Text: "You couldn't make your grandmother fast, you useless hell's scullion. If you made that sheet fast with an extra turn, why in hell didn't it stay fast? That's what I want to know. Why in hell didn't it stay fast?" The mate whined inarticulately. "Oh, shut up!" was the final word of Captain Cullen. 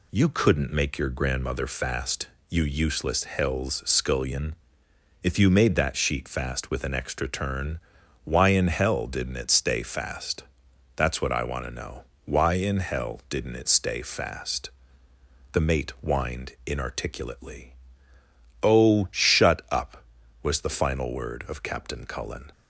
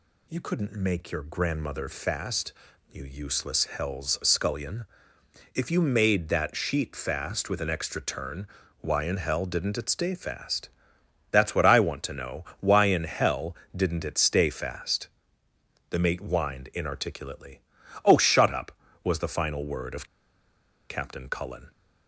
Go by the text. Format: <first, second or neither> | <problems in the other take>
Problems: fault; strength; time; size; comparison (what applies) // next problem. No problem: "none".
first | pauses between "hell" and "didn't"; slight; at 13.5 s; 0.18 s long // pauses between "of" and "Captain"; noticeable; at 20.0 s; 0.85 s long